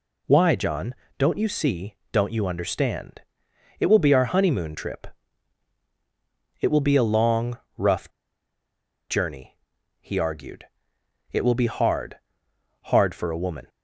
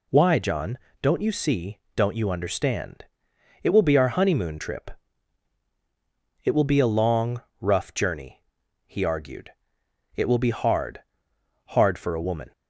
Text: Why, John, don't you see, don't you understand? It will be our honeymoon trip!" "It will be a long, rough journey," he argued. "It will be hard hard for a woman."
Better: second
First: pauses between "rough" and "journey"; at 8.0 s; 1.0 s long // pauses between "hard" and "hard"; noticeable; at 12.1 s; 0.70 s long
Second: pauses between "hard" and "hard"; noticeable; at 11.0 s; 0.70 s long

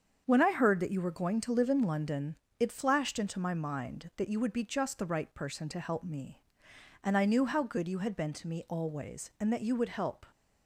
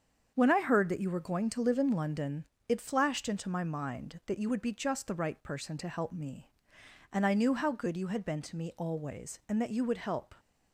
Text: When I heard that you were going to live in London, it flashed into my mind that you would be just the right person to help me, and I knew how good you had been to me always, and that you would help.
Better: neither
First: starts louder than the rest; strong; until 1.2 s; 7.5 dB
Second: starts louder than the rest; strong; until 1.3 s; 7.5 dB

